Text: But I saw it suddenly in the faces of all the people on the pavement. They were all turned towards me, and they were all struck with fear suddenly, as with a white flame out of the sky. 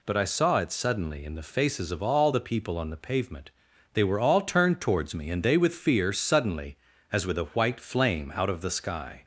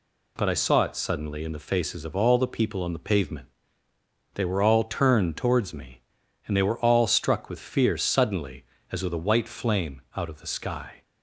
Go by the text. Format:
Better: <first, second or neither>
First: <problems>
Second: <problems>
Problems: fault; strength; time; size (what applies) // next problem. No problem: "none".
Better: second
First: skips "were all struck"; at 5.5 s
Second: none